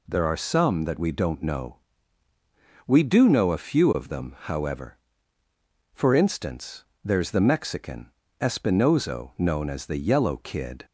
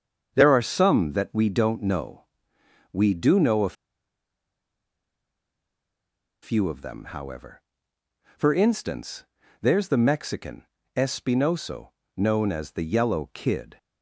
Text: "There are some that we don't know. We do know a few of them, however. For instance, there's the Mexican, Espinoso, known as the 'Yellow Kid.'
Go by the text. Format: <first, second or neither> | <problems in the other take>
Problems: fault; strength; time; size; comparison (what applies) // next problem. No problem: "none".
first | starts louder than the rest; strong; until 1.3 s; 7 dB // pauses between "a" and "few"; strong; at 3.7 s; 2.6 s long